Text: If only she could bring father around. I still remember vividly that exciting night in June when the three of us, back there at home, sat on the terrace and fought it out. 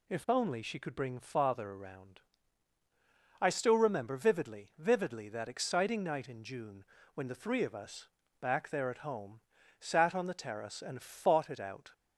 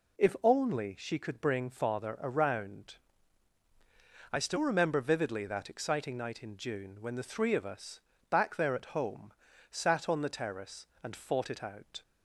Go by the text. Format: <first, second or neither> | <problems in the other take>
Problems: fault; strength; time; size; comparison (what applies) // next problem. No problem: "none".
second | says "vividly" twice; at 4.7 s // pauses between "June" and "when"; slight; at 6.8 s; 0.32 s long